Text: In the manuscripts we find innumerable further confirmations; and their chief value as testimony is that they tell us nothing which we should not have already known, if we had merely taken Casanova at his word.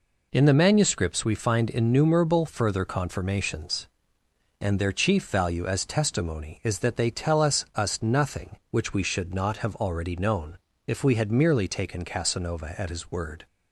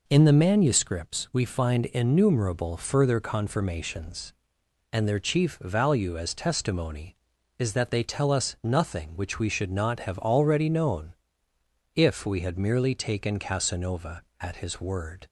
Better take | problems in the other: second | says "us" twice; at 7.7 s

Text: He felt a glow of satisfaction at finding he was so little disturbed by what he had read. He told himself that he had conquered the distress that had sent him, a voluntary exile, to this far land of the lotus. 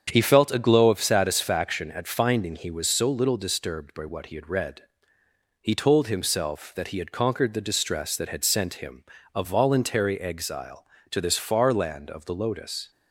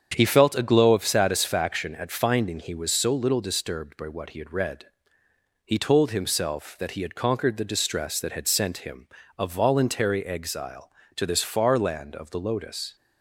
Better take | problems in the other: neither | starts louder than the rest; strong; the same in both

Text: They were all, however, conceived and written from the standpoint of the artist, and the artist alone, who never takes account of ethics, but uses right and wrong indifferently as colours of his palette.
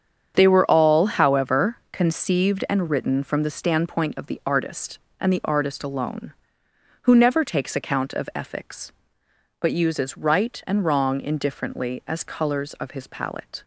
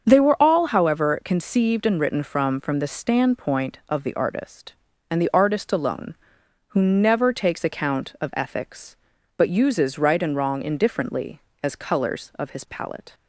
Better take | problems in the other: first | starts louder than the rest; until 1.0 s; 7 dB; strong in the first // says "from" twice; at 2.6 s

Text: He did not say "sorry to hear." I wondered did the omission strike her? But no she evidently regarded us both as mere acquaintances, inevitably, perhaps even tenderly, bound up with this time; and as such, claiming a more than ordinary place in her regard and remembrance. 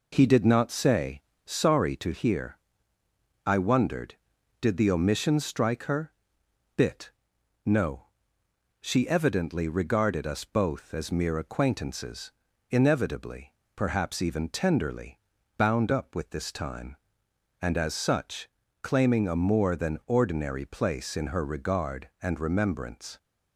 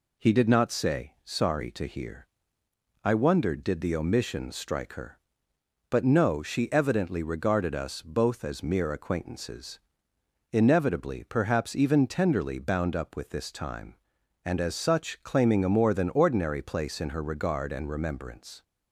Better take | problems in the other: second | pauses between "say" and "sorry"; slight; at 1.2 s; 0.22 s long // says "Bit" for "But"; at 6.7 s // pauses between "no" and "she"; noticeable; at 8.0 s; 0.76 s long

